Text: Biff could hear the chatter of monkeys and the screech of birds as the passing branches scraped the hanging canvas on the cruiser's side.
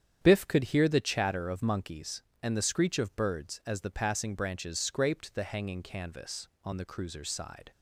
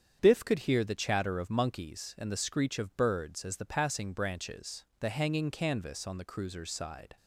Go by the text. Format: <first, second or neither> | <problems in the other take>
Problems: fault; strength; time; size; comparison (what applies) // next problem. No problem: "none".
first | starts louder than the rest; strong; until 1.2 s; 8 dB; strong in the first // skips "scraped"; at 4.9 s